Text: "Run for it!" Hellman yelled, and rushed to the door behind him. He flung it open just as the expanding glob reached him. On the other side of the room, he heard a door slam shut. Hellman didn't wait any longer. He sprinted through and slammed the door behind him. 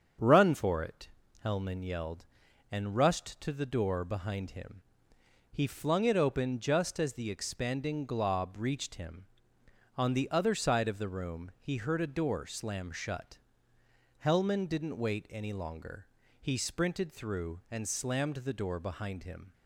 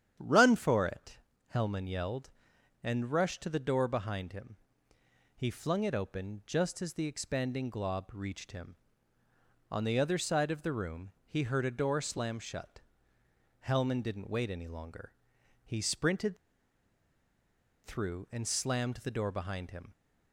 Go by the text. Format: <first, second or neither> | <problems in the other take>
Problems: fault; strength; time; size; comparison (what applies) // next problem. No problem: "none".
first | starts louder than the rest; strong; until 1.5 s; 9.5 dB; strong in the first // pauses between "sprinted" and "through"; strong; at 16.3 s; 1.4 s long